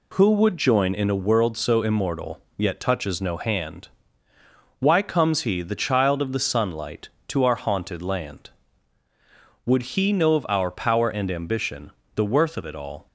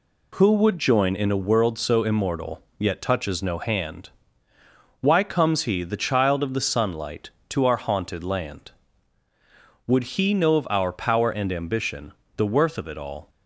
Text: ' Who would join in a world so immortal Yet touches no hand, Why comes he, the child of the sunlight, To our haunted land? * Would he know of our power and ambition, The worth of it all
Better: neither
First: pauses between "immortal" and "Yet"; slight; at 2.4 s; 0.16 s long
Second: pauses between "immortal" and "Yet"; slight; at 2.6 s; 0.16 s long

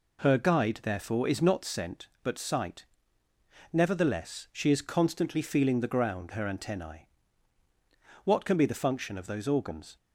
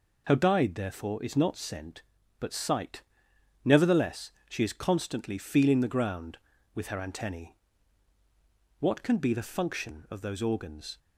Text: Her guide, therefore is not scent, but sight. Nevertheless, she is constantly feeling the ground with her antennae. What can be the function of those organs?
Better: second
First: skips "with"; at 6.3 s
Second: none

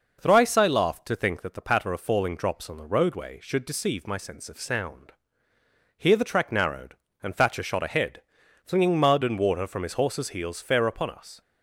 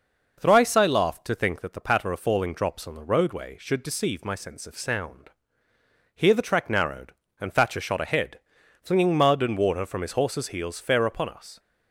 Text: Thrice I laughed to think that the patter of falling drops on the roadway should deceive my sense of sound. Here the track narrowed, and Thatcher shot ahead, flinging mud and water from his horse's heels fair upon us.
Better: neither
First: none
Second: none

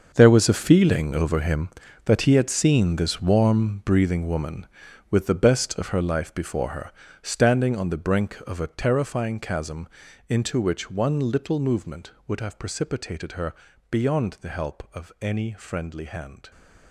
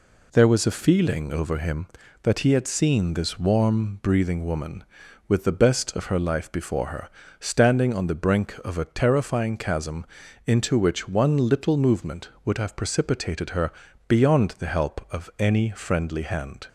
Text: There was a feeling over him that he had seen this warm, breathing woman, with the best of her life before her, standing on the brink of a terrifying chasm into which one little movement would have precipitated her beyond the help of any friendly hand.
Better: second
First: gets quieter; strong; throughout; 13.5 dB // pauses between "chasm" and "into"; at 9.8 s; 0.40 s long // pauses between "her" and "beyond"; slight; at 13.5 s; 0.36 s long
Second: pauses between "chasm" and "into"; at 10.0 s; 0.40 s long // pauses between "her" and "beyond"; slight; at 13.7 s; 0.36 s long

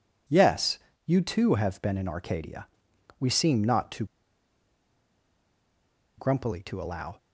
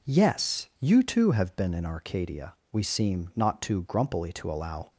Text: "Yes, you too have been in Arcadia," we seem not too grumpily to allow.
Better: second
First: pauses between "too" and "grumpily"; strong; at 4.0 s; 2.1 s long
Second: none

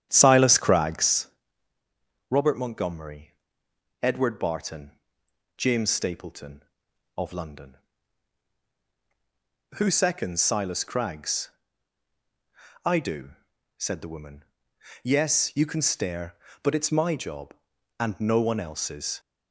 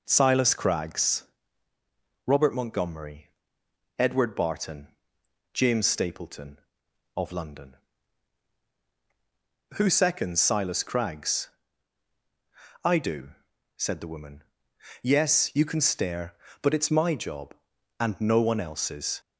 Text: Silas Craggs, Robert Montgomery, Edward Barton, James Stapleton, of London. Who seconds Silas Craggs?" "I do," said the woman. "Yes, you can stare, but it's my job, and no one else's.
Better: second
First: starts louder than the rest; strong; until 1.3 s; 9.5 dB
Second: none

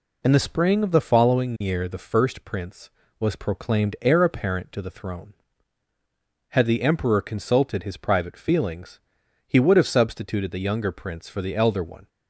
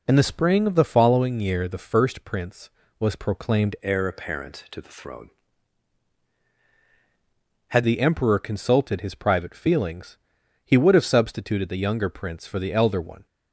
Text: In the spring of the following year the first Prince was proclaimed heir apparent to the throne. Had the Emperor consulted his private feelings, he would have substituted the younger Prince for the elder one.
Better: first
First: none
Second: changes voice from "heir" to "Had"; from 3.8 to 7.8 s; 4.0 s long

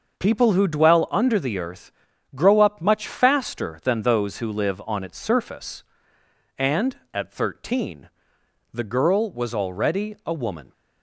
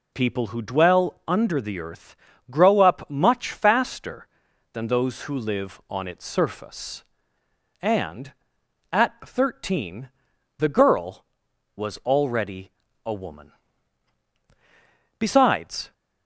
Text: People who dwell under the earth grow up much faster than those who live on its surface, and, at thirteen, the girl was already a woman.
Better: first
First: pauses between "earth" and "grow"; at 1.9 s; 0.42 s long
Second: pauses between "earth" and "grow"; slight; at 2.1 s; 0.36 s long // pauses between "already" and "a"; slight; at 12.7 s; 0.34 s long // goes on to say "Besides"; noticeable; from 15.1 s on; 0.74 s long

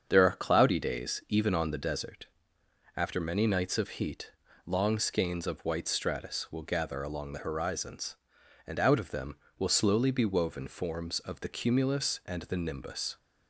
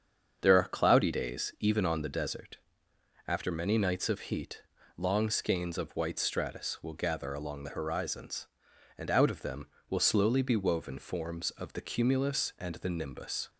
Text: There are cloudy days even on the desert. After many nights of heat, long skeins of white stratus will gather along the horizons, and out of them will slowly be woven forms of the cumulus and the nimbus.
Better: neither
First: starts louder than the rest; strong; until 1.0 s; 7.5 dB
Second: starts louder than the rest; strong; until 1.4 s; 7.5 dB

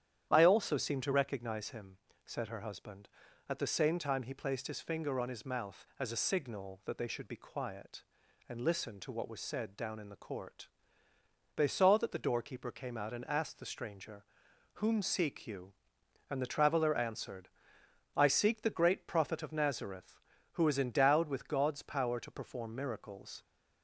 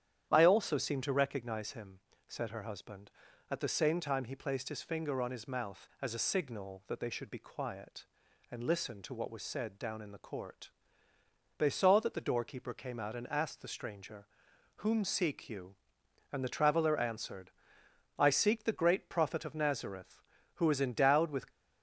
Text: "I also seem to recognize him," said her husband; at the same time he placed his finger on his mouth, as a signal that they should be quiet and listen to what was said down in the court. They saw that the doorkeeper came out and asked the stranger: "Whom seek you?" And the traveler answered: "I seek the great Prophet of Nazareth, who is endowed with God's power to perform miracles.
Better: first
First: starts louder than the rest; strong; until 1.3 s; 10 dB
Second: starts louder than the rest; strong; until 1.3 s; 10 dB // stops before "God's power to perform miracles"; at 21.5 s

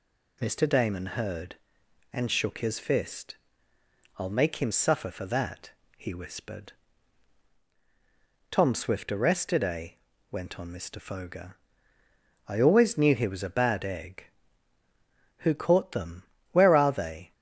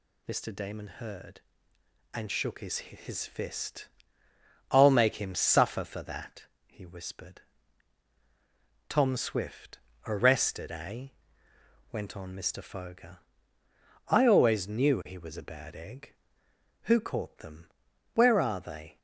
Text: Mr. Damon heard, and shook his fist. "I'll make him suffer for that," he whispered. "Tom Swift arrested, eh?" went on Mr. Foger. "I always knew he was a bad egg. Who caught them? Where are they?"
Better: first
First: none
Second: says "his" twice; at 2.7 s // pauses between "Swift" and "arrested"; slight; at 9.7 s; 0.28 s long

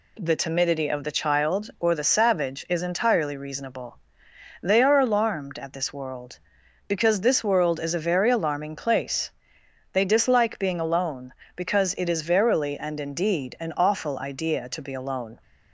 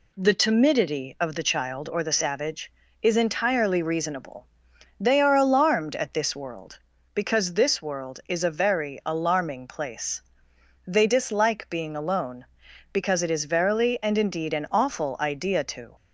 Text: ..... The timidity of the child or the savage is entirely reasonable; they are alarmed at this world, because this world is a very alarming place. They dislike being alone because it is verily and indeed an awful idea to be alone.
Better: first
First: none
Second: stops before "be alone"; at 15.9 s

